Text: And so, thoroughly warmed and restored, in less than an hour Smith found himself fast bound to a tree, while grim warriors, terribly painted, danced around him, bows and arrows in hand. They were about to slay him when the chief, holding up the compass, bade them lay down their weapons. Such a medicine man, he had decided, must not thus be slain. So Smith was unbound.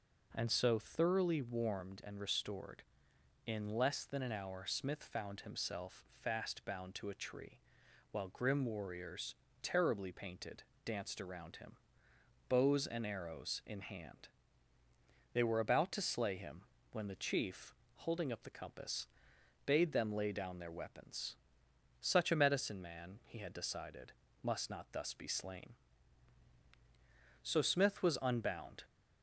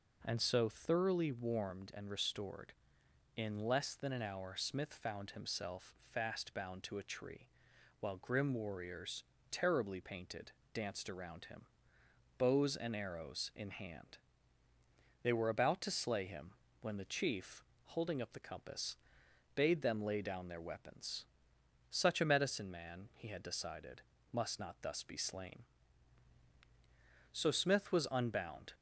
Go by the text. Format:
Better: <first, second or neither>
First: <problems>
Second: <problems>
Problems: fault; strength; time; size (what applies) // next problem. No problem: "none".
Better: neither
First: pauses between "him" and "when"; slight; at 16.6 s; 0.30 s long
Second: pauses between "him" and "when"; slight; at 16.5 s; 0.30 s long